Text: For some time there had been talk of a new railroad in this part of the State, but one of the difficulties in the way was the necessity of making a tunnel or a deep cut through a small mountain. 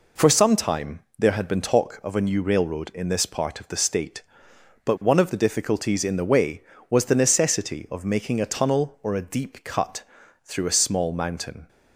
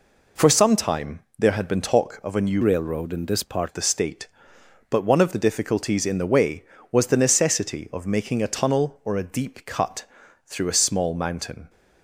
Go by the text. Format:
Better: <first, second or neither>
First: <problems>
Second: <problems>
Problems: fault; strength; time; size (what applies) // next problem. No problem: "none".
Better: first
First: pauses between "time" and "there"; slight; at 1.0 s; 0.18 s long // pauses between "cut" and "through"; at 10.0 s; 0.42 s long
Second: pauses between "time" and "there"; slight; at 1.2 s; 0.18 s long // changes voice from "railroad" to "part"; from 2.6 to 3.6 s; 1.0 s long // pauses between "cut" and "through"; at 10.0 s; 0.42 s long